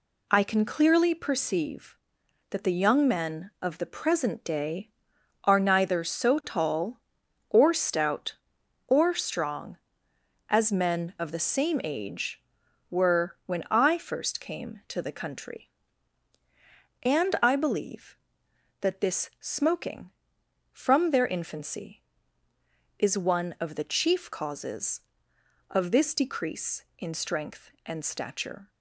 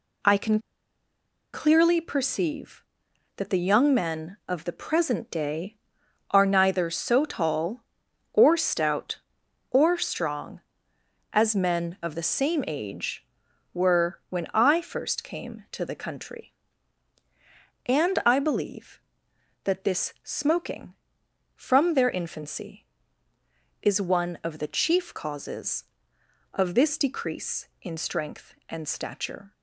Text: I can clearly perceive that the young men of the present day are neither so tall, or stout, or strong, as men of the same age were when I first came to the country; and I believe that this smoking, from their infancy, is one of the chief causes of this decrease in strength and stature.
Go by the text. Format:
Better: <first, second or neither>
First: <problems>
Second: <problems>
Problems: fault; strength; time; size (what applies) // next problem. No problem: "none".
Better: first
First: none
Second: pauses between "can" and "clearly"; noticeable; at 0.5 s; 0.93 s long